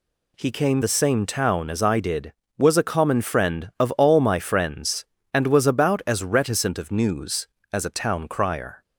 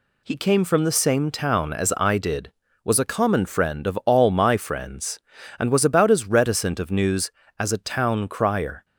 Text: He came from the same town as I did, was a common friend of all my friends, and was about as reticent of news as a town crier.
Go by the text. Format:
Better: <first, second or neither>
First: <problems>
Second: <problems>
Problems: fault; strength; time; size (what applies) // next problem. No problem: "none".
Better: second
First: skips "from"; at 0.8 s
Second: none